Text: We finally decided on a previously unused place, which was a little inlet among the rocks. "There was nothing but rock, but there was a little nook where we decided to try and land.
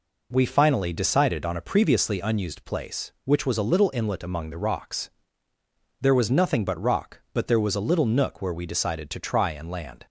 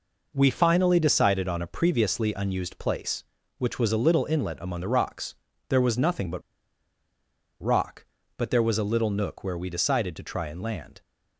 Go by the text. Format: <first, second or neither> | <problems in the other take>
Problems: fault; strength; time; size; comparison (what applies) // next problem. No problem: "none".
first | pauses between "but" and "rock"; at 6.4 s; 1.1 s long